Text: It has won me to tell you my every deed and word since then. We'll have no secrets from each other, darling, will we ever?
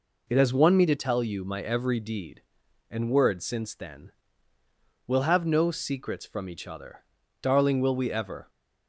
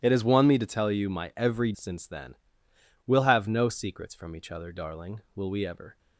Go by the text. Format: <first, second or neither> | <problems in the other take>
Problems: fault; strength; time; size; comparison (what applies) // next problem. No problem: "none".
first | starts louder than the rest; strong; until 1.0 s; 13.5 dB // skips "deed and word"; at 1.7 s